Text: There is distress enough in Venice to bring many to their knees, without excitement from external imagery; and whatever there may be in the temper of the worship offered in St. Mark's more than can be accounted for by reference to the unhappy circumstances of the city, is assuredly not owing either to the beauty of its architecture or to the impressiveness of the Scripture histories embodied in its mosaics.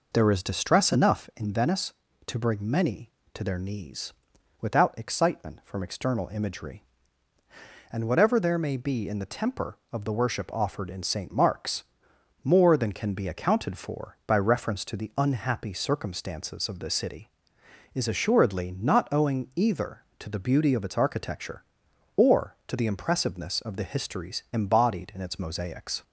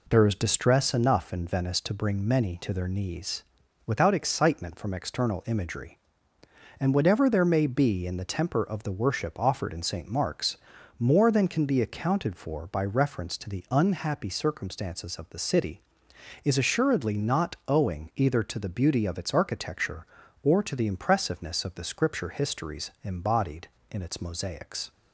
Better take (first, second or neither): second